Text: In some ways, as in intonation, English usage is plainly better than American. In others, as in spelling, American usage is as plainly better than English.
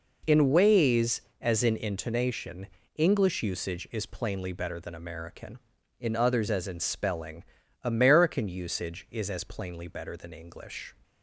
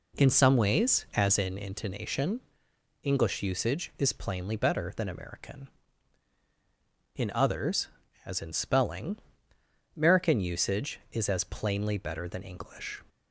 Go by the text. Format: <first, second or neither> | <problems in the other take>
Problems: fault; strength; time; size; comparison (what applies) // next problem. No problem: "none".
second | skips "some"; at 0.5 s